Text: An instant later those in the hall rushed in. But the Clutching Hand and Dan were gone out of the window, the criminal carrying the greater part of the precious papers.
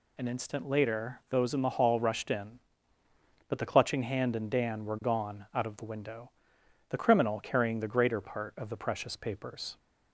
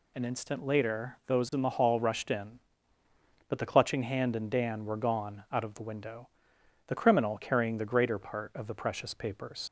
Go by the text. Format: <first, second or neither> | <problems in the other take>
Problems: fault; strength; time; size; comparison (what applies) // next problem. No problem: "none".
first | leaves "papers" unfinished; at 9.6 s; 70 ms